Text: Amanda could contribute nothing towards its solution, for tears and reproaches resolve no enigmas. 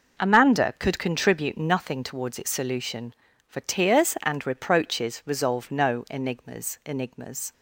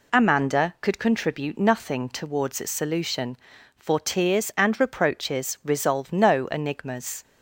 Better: second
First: says "enigmas" twice; at 6.8 s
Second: none

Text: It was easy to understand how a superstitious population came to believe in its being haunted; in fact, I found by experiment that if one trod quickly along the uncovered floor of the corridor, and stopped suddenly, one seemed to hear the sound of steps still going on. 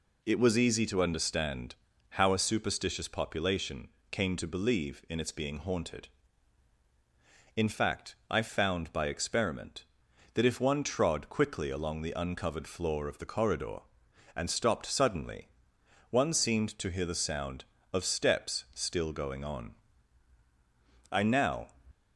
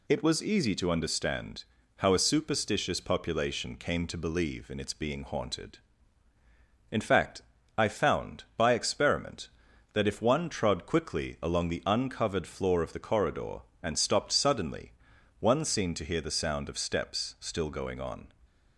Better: second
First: pauses between "understand" and "how"; slight; at 1.7 s; 0.36 s long // pauses between "population" and "came"; slight; at 3.8 s; 0.24 s long // goes on to say "I now"; from 21.1 s on; 0.56 s long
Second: pauses between "understand" and "how"; slight; at 1.6 s; 0.32 s long

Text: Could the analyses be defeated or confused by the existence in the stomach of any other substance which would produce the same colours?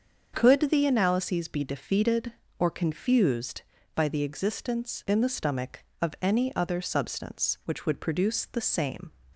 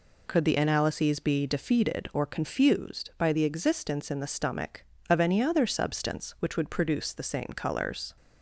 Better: second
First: starts louder than the rest; until 1.3 s; 7 dB // stops before "colours"; at 9.3 s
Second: none

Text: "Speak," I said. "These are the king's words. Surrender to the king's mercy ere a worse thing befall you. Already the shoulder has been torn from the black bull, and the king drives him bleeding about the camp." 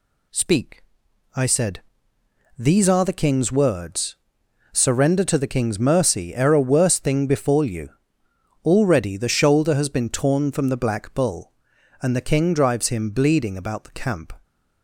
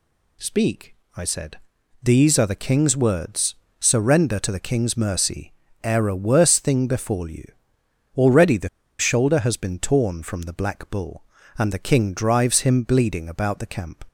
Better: first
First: none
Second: pauses between "mercy" and "ere"; slight; at 5.5 s; 0.32 s long // pauses between "the" and "shoulder"; slight; at 8.6 s; 0.31 s long

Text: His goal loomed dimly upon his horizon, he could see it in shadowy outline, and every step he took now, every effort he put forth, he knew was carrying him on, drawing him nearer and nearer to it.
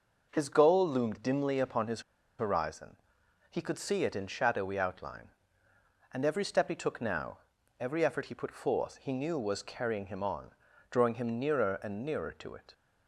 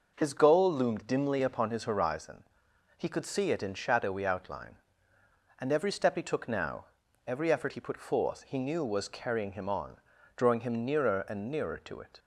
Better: second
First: pauses between "his" and "horizon"; at 2.0 s; 0.37 s long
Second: none

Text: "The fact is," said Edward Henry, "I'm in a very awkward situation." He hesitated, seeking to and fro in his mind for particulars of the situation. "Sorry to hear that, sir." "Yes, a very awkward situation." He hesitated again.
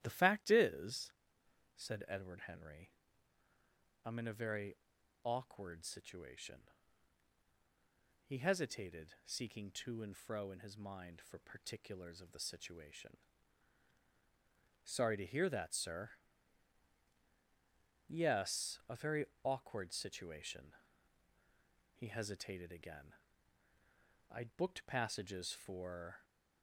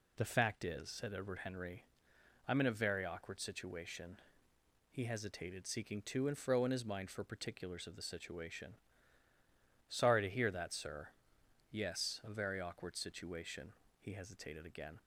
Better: second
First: starts louder than the rest; strong; until 1.0 s; 12 dB // pauses between "very" and "awkward"; noticeable; at 4.7 s; 0.46 s long // pauses between "very" and "awkward"; slight; at 19.2 s; 0.18 s long // goes on to say "I'd booked passages for"; strong; from 24.3 s on; 1.9 s long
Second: none

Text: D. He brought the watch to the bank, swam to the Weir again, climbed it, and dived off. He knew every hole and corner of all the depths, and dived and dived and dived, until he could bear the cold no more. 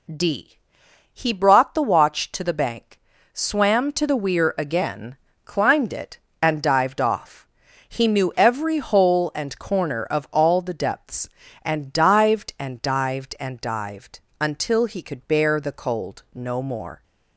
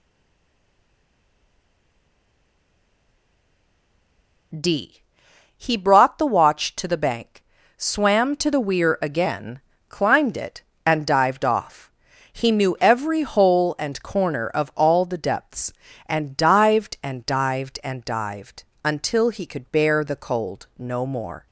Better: first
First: none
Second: stays silent before the first word; strong; until 4.5 s; 4.5 s long

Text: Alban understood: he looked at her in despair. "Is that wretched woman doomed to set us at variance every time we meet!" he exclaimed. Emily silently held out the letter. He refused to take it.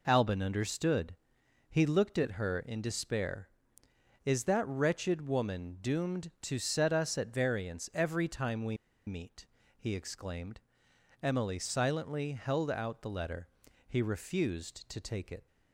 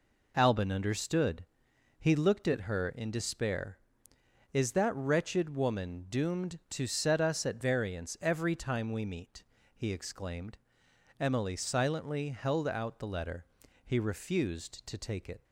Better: second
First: pauses between "we" and "meet"; slight; at 8.7 s; 0.31 s long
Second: none

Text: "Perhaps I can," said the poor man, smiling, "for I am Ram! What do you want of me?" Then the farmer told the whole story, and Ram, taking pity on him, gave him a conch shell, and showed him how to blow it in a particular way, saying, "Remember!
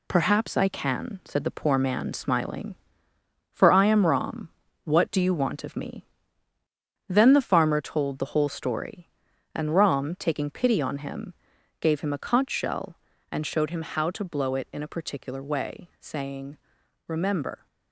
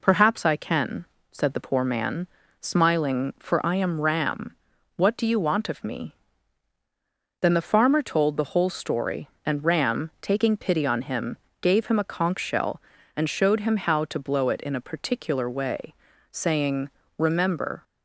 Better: second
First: gets quieter; noticeable; throughout; 5.5 dB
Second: none

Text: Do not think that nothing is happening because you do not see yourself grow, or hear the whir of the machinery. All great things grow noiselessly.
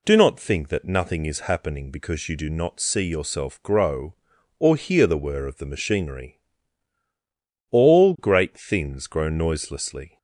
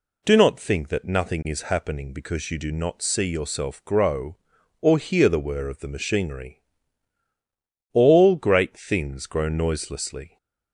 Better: neither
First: none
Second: none

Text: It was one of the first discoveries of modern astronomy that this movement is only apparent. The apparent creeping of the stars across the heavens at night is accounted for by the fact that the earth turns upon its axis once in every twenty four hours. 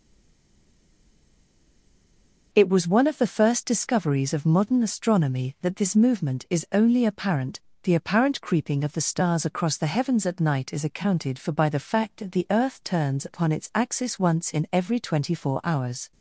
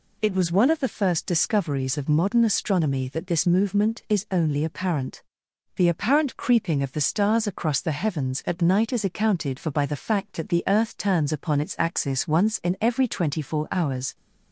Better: second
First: stays silent before the first word; strong; until 2.5 s; 2.5 s long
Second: none

